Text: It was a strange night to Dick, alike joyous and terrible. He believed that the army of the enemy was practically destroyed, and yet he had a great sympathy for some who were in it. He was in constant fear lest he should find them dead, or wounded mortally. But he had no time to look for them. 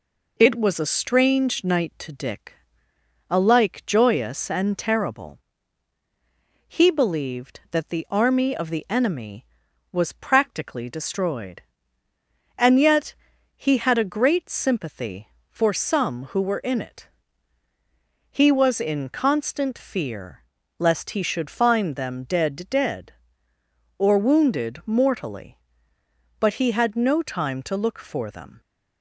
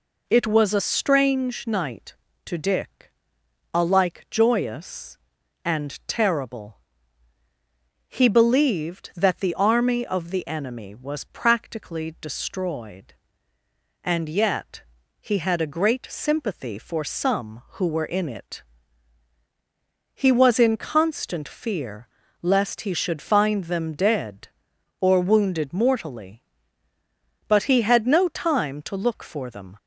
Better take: second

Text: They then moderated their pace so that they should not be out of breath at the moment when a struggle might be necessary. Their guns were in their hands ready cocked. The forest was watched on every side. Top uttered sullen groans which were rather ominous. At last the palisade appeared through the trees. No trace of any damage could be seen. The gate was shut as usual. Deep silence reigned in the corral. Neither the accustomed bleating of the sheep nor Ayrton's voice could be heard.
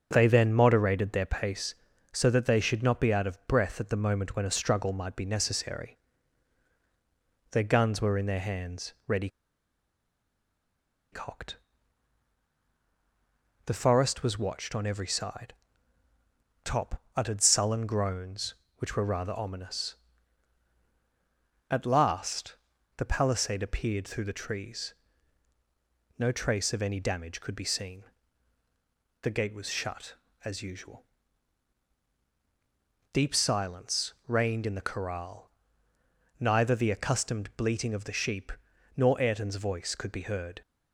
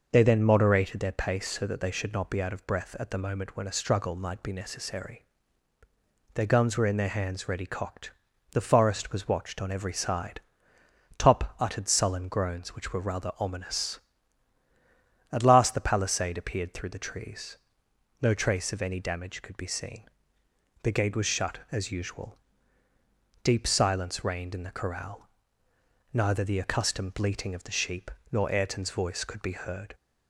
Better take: second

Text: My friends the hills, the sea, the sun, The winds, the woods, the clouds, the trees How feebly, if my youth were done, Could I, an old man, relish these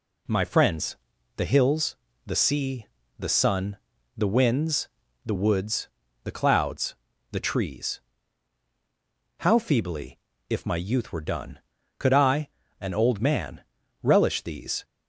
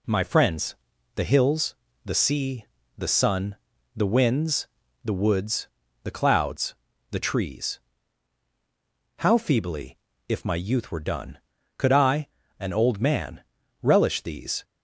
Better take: neither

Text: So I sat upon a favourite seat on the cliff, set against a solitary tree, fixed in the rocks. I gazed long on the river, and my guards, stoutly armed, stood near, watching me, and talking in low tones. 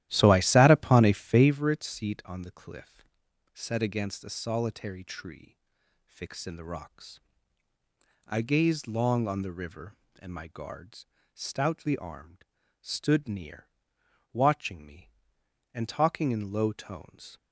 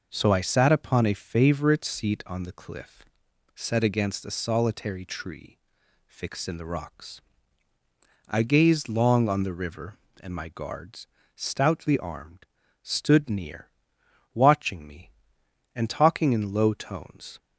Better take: second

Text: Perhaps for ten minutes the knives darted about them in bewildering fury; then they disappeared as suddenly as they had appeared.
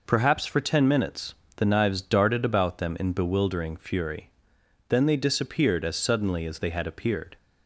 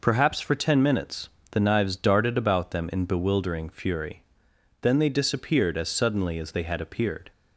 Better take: neither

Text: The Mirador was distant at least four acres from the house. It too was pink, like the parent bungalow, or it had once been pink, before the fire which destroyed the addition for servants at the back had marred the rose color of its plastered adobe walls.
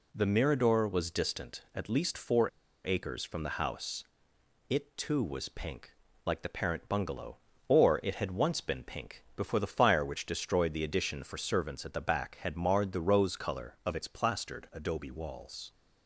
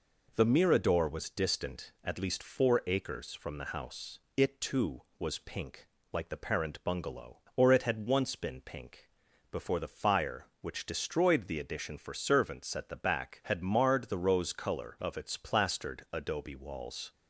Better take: second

